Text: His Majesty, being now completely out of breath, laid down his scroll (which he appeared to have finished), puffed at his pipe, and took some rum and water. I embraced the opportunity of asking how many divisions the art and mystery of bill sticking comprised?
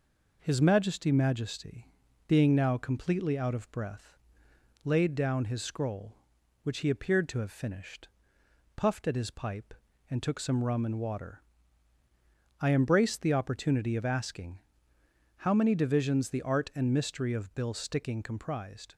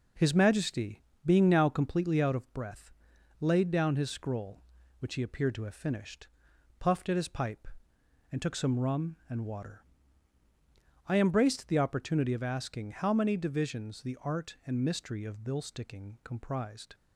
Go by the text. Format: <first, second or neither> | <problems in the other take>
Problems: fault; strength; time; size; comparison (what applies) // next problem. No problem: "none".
second | says "Majesty" twice; at 1.1 s // pauses between "asking" and "how"; noticeable; at 14.5 s; 0.78 s long